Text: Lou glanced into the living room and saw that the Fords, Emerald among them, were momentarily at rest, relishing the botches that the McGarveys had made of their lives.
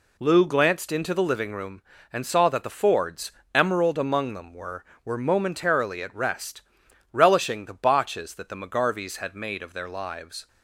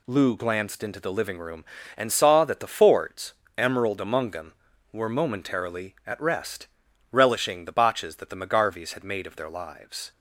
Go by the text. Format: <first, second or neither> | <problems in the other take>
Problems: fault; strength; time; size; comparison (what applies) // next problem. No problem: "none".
second | says "were" twice; at 5.0 s